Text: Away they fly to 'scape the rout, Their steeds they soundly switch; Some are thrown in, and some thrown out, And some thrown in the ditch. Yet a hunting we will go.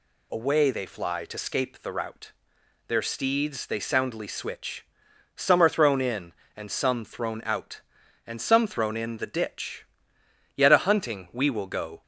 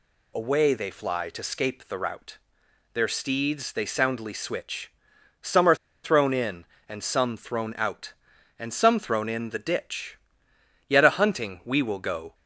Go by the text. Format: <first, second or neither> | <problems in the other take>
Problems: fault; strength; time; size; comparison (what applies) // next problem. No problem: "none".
first | pauses between "are" and "thrown"; slight; at 5.7 s; 0.27 s long